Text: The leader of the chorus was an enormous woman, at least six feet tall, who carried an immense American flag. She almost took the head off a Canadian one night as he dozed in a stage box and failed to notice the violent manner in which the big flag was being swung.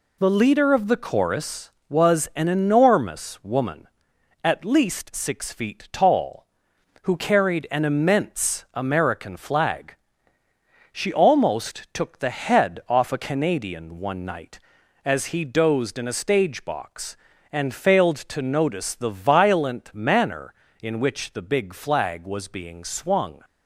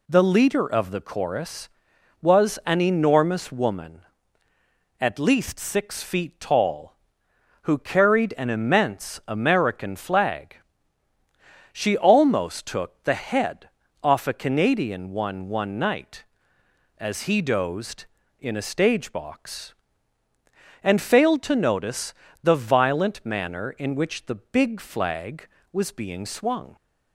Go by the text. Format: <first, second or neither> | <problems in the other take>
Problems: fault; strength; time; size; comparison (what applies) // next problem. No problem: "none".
first | pauses between "head" and "off"; slight; at 13.6 s; 0.34 s long // says "one" twice; at 15.4 s // pauses between "notice" and "the"; slight; at 22.1 s; 0.30 s long